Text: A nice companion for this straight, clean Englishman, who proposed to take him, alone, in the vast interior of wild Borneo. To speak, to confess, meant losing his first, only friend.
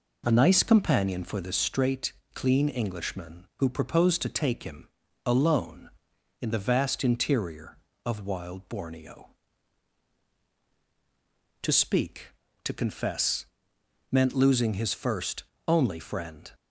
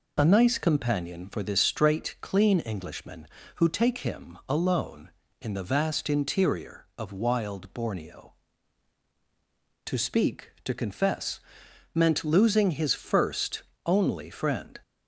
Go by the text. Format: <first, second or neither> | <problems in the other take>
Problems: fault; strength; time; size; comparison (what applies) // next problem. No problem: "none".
first | skips "proposed to"; at 3.6 s